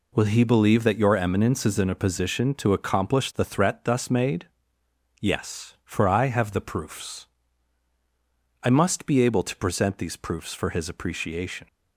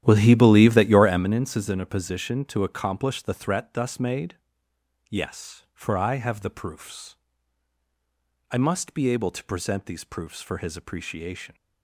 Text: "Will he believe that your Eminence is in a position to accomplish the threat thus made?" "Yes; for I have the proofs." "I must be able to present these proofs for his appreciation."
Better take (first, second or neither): first